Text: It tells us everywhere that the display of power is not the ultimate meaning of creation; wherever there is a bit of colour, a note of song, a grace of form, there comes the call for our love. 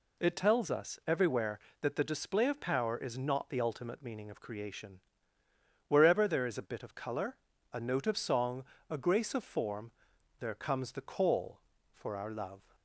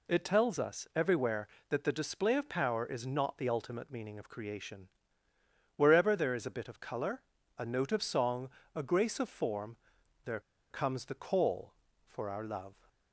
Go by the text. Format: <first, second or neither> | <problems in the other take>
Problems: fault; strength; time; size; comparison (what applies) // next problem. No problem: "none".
first | pauses between "there" and "comes"; slight; at 10.3 s; 0.30 s long